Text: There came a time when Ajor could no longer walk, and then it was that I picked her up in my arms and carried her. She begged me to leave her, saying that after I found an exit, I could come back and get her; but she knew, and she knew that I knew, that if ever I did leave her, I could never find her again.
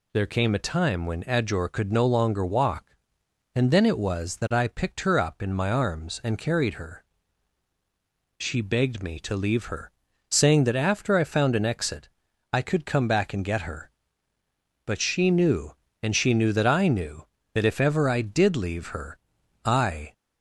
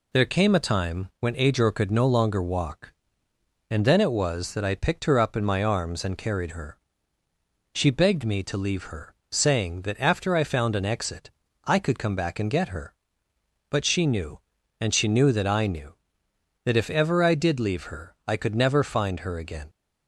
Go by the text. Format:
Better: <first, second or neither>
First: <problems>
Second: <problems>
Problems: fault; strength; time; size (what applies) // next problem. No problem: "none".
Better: second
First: stops before "could never find her again"; at 20.1 s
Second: none